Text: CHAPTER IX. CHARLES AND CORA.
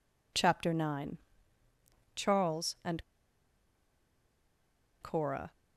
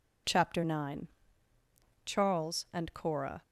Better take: second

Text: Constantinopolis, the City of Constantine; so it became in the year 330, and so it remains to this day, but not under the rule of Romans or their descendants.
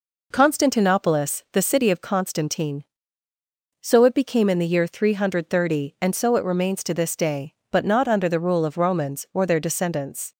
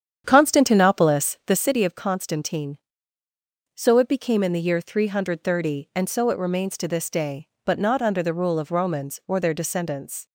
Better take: first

